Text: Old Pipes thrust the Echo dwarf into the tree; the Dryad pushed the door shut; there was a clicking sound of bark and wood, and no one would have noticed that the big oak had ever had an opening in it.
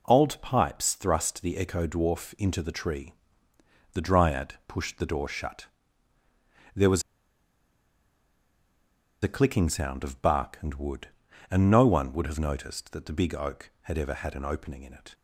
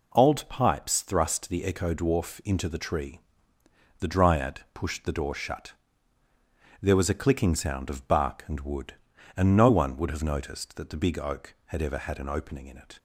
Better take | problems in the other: second | pauses between "was" and "a"; strong; at 7.0 s; 2.2 s long

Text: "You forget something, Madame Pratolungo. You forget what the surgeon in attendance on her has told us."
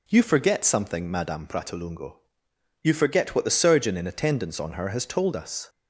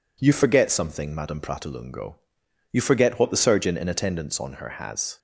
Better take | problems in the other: first | stops before "told us"; at 5.1 s

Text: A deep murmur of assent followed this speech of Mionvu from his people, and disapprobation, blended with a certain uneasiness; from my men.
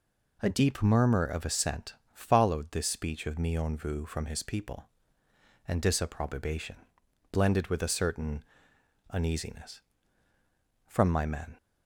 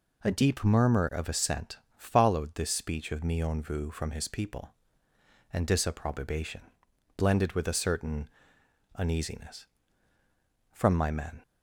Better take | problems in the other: neither | pauses between "assent" and "followed"; slight; the same in both // pauses between "certain" and "uneasiness"; noticeable; the same in both

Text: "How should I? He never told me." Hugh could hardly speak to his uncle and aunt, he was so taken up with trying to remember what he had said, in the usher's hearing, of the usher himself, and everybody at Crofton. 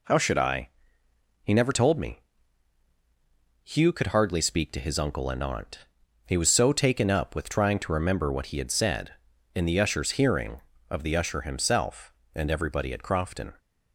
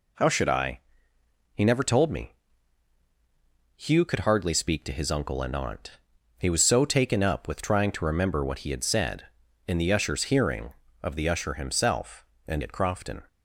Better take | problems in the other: first | skips "everybody"; at 12.6 s

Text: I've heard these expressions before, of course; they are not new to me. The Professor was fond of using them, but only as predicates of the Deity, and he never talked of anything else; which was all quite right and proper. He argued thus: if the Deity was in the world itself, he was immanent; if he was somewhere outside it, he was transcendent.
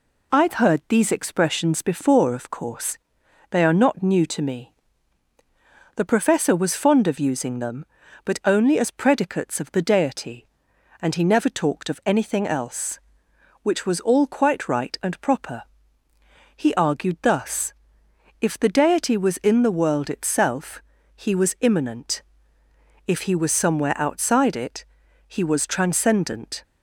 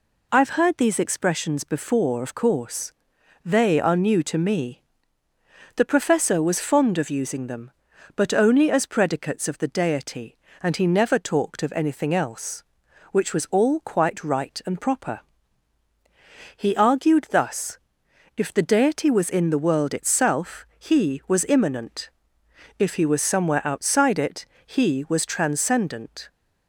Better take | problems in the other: first | skips "not"; at 3.9 s

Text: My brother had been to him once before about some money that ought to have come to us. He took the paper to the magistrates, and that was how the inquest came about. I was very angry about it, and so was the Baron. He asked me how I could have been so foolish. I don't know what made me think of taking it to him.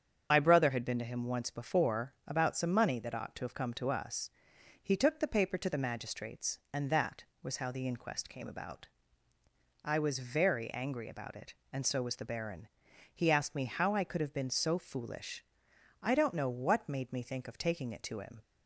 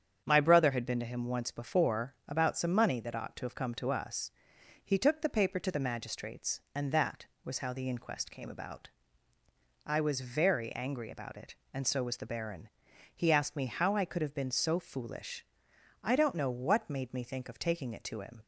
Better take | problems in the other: second | loses the start of "My"; at 0.3 s; 60 ms // starts louder than the rest; strong; until 1.3 s; 8 dB; strong in the second

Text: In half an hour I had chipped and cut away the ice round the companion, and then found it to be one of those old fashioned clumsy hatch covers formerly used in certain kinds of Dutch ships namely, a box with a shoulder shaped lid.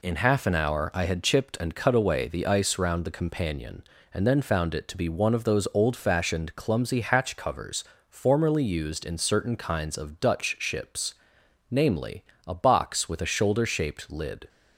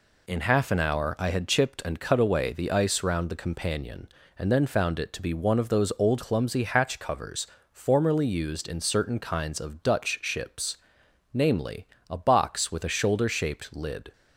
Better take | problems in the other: first | skips "fashioned"; at 6.2 s // pauses between "covers" and "formerly"; slight; at 7.4 s; 0.24 s long; slight in the first // pauses between "ships" and "namely"; noticeable; at 10.7 s; 0.56 s long; noticeable in the first

